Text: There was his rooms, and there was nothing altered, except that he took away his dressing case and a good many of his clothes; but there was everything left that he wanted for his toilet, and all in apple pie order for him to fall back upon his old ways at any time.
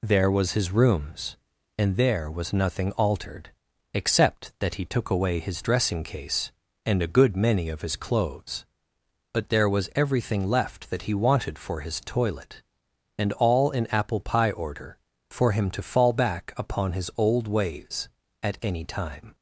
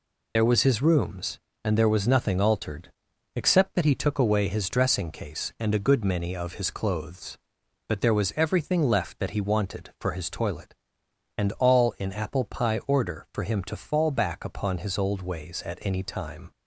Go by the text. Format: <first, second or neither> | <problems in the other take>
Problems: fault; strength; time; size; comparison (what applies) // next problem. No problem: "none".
first | loses the start of "There"; at 0.3 s; 25 ms